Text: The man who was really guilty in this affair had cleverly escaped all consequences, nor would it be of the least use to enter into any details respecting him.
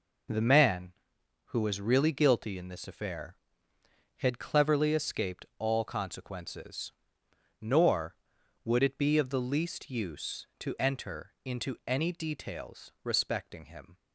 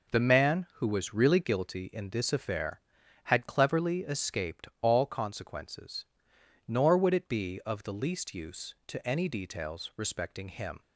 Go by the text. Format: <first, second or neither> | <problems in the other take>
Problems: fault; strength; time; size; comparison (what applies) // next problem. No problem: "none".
first | skips "enter into"; at 9.0 s